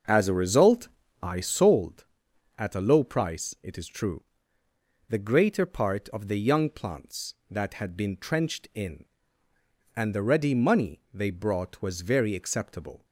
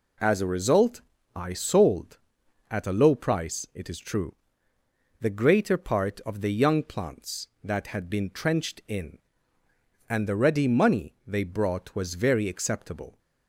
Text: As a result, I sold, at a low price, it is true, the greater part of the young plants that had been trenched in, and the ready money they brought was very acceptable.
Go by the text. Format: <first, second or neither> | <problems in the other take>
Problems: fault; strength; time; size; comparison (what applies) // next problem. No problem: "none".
second | starts louder than the rest; until 1.8 s; 6.5 dB